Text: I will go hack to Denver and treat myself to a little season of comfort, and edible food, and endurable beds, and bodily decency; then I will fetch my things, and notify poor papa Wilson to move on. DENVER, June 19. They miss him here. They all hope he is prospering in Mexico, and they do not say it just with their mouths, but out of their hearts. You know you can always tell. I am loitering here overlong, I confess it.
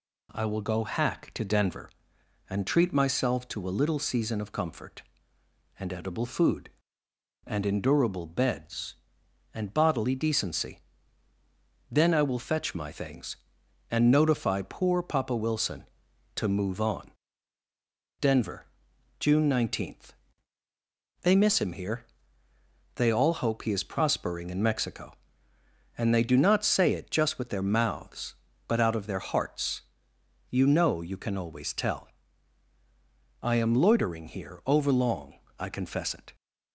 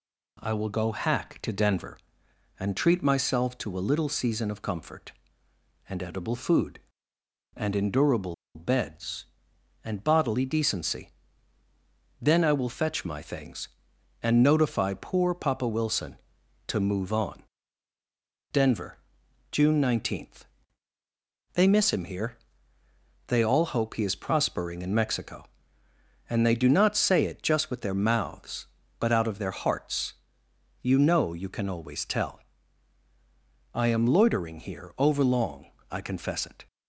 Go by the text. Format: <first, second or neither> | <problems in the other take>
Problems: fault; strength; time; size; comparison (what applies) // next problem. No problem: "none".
first | pauses between "endurable" and "beds"; slight; at 8.3 s; 0.20 s long